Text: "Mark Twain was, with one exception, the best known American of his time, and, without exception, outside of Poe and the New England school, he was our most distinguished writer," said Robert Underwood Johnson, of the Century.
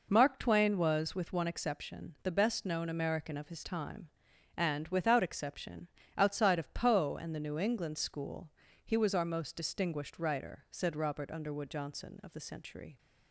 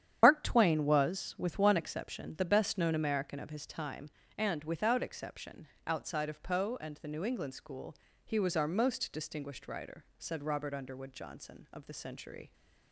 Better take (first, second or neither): first